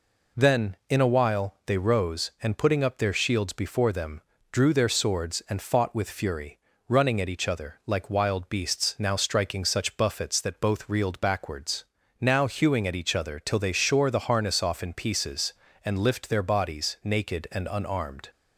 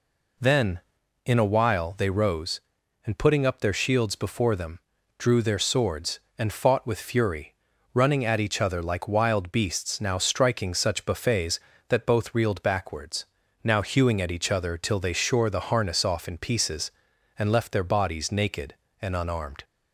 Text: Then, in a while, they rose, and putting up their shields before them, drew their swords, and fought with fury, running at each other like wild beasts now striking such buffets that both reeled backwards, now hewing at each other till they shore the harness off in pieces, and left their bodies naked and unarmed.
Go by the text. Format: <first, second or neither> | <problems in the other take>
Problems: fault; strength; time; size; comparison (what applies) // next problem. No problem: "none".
second | says "lift" for "left"; at 15.9 s